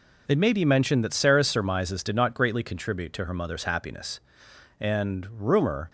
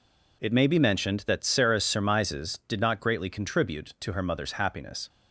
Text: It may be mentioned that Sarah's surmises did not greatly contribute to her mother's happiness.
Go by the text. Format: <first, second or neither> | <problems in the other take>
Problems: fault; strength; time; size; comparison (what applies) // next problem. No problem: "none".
second | goes on to say "And rumor"; noticeable; from 4.7 s on; 1.1 s long